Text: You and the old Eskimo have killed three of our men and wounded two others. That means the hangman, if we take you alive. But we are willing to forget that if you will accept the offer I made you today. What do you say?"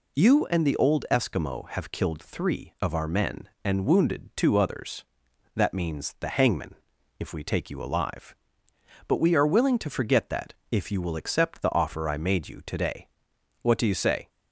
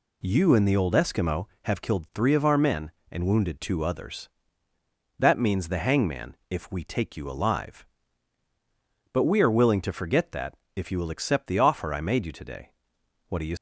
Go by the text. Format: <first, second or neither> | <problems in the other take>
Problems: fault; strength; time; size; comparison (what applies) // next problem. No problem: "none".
first | pauses between "that" and "if"; slight; at 10.5 s; 0.20 s long; slight in the first // stops before "say"; at 13.5 s